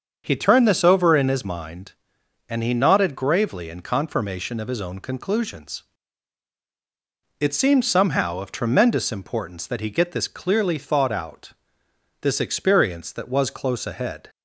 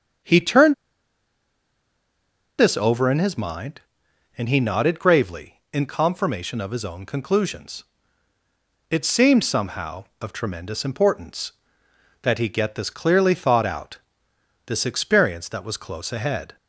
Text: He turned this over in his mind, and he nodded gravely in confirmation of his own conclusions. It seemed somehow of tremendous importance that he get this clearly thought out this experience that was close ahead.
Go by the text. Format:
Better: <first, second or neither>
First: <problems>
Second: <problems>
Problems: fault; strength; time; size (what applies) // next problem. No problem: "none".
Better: first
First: starts louder than the rest; until 1.2 s; 7 dB // pauses between "out" and "this"; noticeable; at 11.5 s; 0.70 s long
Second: starts louder than the rest; strong; until 3.1 s; 7 dB // pauses between "turned" and "this"; strong; at 0.7 s; 1.8 s long // pauses between "out" and "this"; noticeable; at 13.9 s; 0.68 s long